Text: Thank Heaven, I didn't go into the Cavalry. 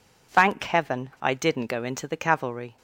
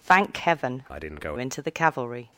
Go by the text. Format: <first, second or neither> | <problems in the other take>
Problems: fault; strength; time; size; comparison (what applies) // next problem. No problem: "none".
first | changes voice from "I" to "go"; from 0.9 to 1.3 s; 0.4 s long